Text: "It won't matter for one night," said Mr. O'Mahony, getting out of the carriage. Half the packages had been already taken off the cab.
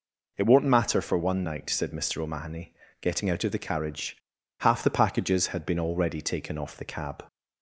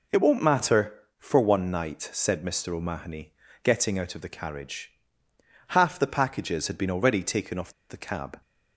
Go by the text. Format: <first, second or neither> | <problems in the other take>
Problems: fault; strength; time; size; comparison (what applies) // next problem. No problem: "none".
first | pauses between "off" and "the"; slight; at 7.7 s; 0.17 s long